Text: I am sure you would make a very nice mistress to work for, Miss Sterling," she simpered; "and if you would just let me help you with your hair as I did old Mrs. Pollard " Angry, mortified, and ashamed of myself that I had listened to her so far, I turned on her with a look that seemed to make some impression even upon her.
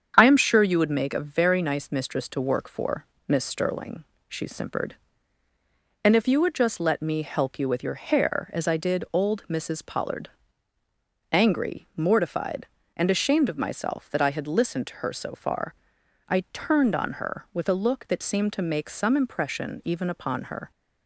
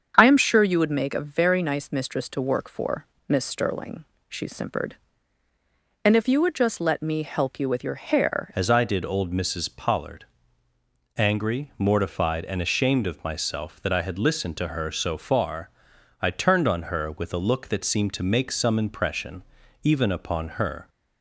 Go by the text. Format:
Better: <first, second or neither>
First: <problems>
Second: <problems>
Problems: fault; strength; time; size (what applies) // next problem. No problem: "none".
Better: first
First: starts louder than the rest; strong; until 1.1 s; 8 dB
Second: starts louder than the rest; strong; until 1.1 s; 7.5 dB // changes voice at "as"; from 8.5 s on; 12.3 s long // pauses between "impression" and "even"; at 19.4 s; 0.40 s long